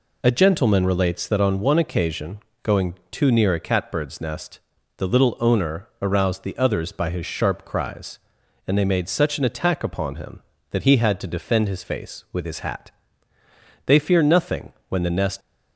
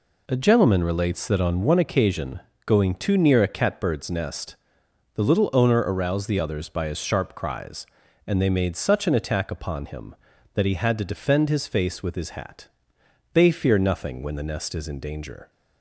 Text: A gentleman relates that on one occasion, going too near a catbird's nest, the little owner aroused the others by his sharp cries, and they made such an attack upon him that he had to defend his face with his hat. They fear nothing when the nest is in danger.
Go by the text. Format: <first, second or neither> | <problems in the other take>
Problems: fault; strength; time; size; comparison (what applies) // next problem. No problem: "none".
second | pauses between "going" and "too"; slight; at 2.9 s; 0.18 s long // pauses between "owner" and "aroused"; slight; at 5.8 s; 0.16 s long // pauses between "nothing" and "when"; slight; at 14.7 s; 0.18 s long // stops before "is in danger"; at 15.4 s